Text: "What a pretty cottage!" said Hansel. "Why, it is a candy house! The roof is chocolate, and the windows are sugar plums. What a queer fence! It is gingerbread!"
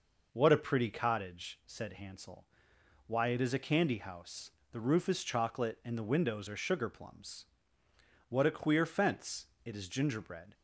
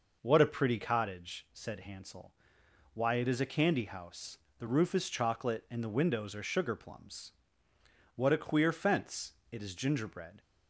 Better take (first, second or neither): neither